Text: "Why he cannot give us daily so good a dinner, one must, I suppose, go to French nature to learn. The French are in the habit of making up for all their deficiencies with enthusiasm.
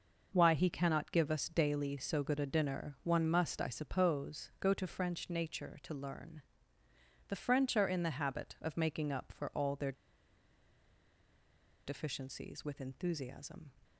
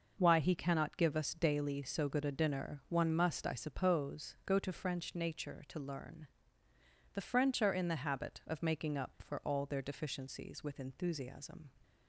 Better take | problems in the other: second | pauses between "their" and "deficiencies"; strong; at 9.9 s; 1.9 s long

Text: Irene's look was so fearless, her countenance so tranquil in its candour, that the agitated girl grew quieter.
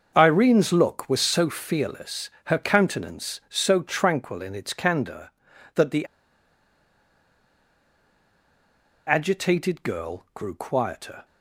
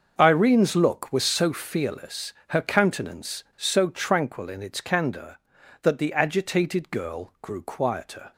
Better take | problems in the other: second | starts louder than the rest; until 1.1 s; 6.5 dB; also in the second // pauses between "the" and "agitated"; strong; at 6.0 s; 3.0 s long

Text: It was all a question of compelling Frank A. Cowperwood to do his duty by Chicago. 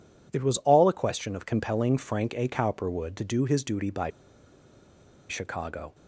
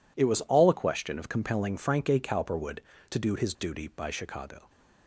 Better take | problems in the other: second | pauses between "by" and "Chicago"; at 4.1 s; 1.1 s long

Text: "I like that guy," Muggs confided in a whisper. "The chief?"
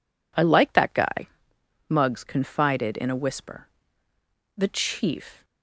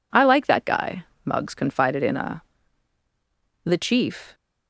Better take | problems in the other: first | skips "whisper"; at 3.0 s

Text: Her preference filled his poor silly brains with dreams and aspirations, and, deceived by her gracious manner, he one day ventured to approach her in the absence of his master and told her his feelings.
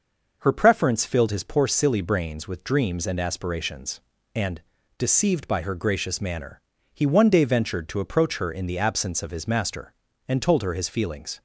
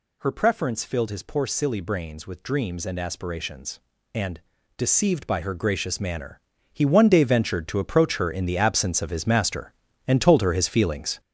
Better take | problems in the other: first | gets louder; strong; throughout; 8 dB

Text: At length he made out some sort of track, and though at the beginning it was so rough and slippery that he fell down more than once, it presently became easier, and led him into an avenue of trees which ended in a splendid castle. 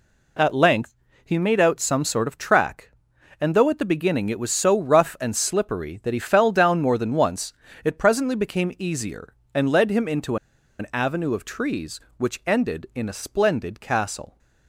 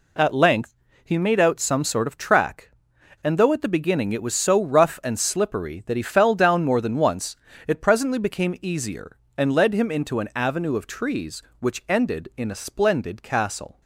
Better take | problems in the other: second | pauses between "length" and "he"; slight; at 0.9 s; 0.30 s long; slight in the second // pauses between "into" and "an"; at 10.3 s; 0.43 s long

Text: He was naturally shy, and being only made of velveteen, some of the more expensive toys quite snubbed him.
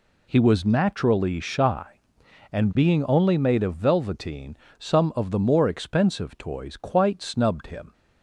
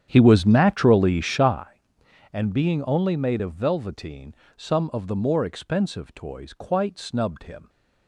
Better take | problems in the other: first | starts louder than the rest; strong; until 1.7 s; 9 dB

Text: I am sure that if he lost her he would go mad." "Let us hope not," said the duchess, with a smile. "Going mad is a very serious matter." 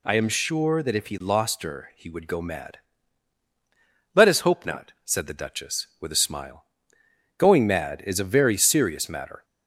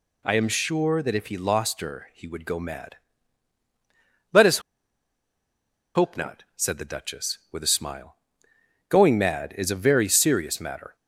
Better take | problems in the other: first | pauses between "us" and "hope"; strong; at 4.6 s; 1.3 s long

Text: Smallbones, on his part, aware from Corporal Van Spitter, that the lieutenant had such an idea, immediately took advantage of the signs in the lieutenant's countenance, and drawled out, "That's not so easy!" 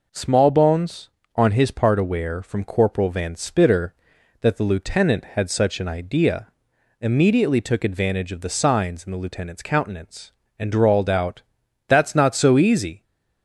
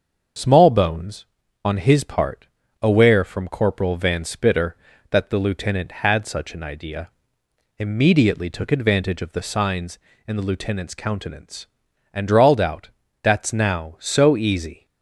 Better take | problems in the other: first | starts louder than the rest; until 1.7 s; 6.5 dB // says "now" for "not"; at 13.5 s

